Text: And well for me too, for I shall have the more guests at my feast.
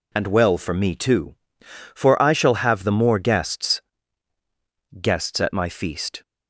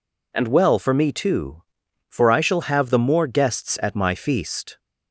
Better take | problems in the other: second | says "guests" twice; at 4.9 s

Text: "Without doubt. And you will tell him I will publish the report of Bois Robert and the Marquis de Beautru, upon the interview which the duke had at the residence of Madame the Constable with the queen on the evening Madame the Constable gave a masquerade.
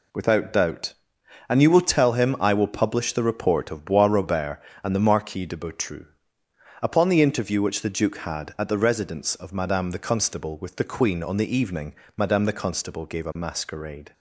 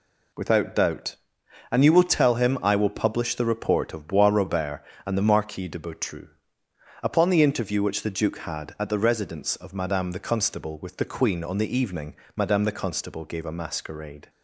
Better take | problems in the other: neither | pauses between "evening" and "Madame"; slight; the same in both

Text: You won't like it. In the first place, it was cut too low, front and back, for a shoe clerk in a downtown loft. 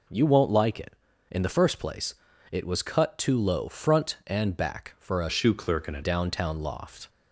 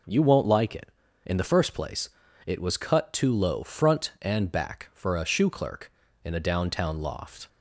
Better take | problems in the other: second | changes voice from "shoe" to "a"; from 5.3 to 6.0 s; 0.7 s long

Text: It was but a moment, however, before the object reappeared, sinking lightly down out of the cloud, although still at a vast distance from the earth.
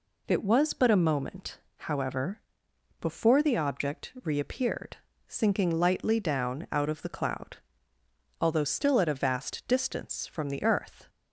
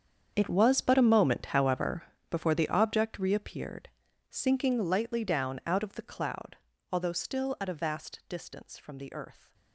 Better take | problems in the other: first | gets quieter; strong; throughout; 16 dB

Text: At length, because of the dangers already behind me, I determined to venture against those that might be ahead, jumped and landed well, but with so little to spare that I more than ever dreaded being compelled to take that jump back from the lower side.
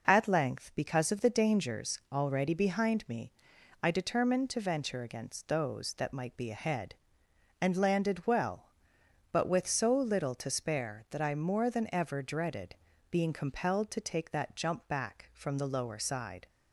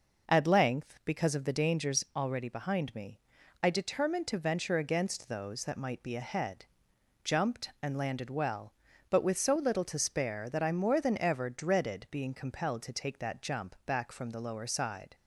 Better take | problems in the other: second | skips "jumped"; at 7.2 s // pauses between "dreaded" and "being"; slight; at 12.7 s; 0.34 s long

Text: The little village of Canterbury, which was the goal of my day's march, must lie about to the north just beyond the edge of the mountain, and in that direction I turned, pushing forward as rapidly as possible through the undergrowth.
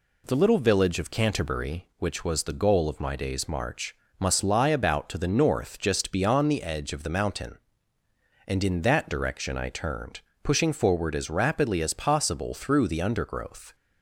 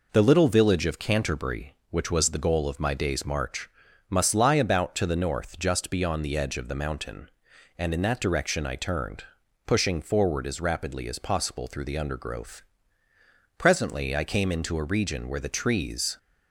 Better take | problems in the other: first | goes on to say "Presently I came into a region where the trees"; strong; from 13.5 s on; 2.5 s long

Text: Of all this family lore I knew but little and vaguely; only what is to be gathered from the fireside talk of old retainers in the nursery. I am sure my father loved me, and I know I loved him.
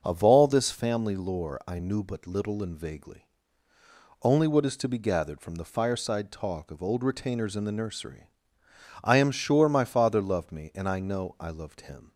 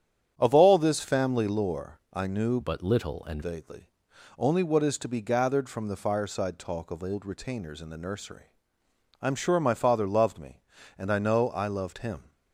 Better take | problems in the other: first | starts louder than the rest; strong; until 1.3 s; 9 dB // changes voice from "but" to "and"; from 2.6 to 3.4 s; 0.8 s long

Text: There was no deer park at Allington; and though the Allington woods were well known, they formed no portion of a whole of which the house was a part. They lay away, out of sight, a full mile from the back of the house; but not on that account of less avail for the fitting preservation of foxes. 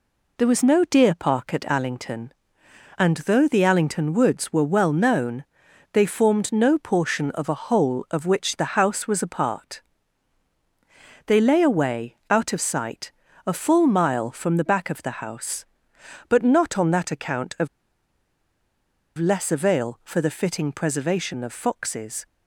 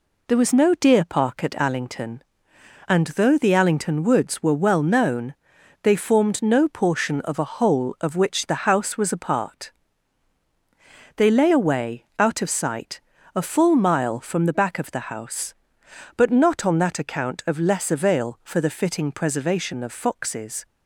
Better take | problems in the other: second | pauses between "of" and "less"; strong; at 17.6 s; 1.5 s long

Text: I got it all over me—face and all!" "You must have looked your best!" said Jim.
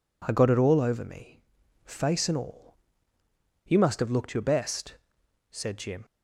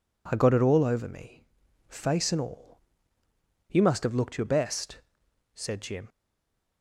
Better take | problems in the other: first | stays silent after the last word; slight; from 6.0 s on; 0.8 s long

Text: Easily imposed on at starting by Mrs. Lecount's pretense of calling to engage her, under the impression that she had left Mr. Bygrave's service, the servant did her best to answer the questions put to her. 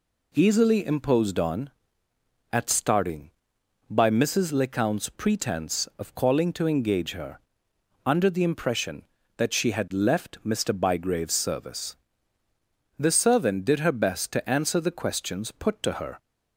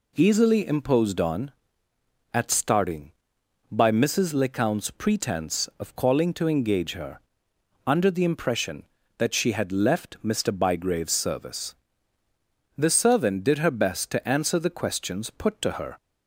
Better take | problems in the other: neither | none

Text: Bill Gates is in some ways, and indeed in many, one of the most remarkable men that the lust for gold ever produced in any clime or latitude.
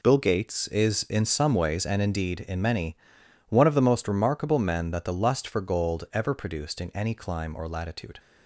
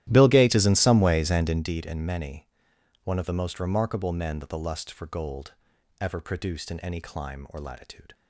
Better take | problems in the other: first | starts louder than the rest; strong; until 1.8 s; 13.5 dB // pauses between "gold" and "ever"; noticeable; at 5.5 s; 0.48 s long

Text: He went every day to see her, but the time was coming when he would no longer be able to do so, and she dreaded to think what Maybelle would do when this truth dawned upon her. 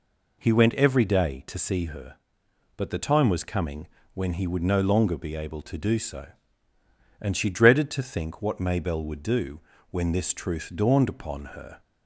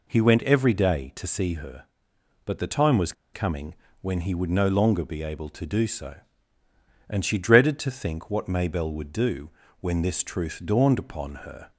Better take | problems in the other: first | pauses between "was" and "coming"; slight; at 3.1 s; 0.21 s long // pauses between "coming" and "when"; slight; at 3.7 s; 0.26 s long; slight in the first // pauses between "do" and "when"; slight; at 9.4 s; 0.30 s long; slight in the first

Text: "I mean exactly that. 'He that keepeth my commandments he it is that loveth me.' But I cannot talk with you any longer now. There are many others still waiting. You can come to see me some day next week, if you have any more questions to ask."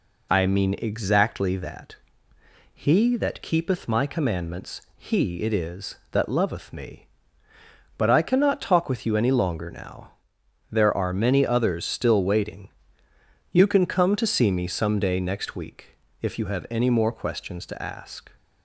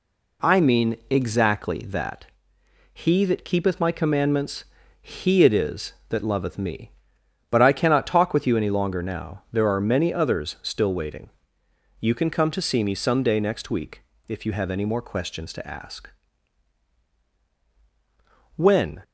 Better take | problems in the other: first | pauses between "commandments" and "he"; at 4.6 s; 0.38 s long // goes on to say "When"; slight; from 18.5 s on; 0.46 s long

